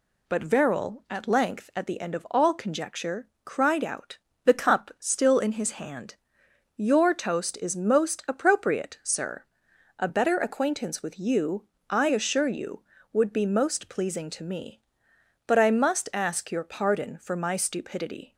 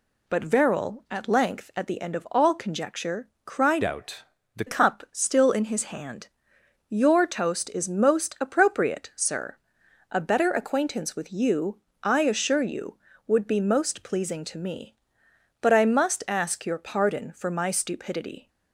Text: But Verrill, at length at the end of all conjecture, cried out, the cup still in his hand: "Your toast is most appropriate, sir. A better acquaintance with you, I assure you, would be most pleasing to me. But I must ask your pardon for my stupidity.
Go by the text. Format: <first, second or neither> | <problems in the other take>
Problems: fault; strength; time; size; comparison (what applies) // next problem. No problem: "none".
first | changes voice from "out" to "the"; from 3.8 to 4.6 s; 0.8 s long